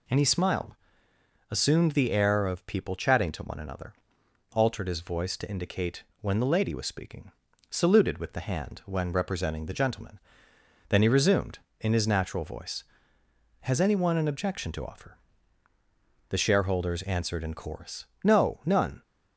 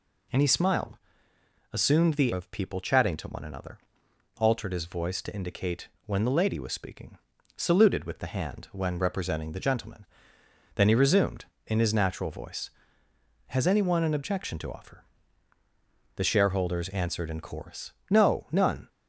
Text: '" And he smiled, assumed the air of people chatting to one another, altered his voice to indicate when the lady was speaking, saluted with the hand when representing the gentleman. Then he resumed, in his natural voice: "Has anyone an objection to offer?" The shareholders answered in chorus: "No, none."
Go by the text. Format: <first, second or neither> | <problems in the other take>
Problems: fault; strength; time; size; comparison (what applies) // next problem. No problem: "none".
first | skips "air"; at 2.3 s // pauses between "indicate" and "when"; slight; at 5.8 s; 0.18 s long; slight in the first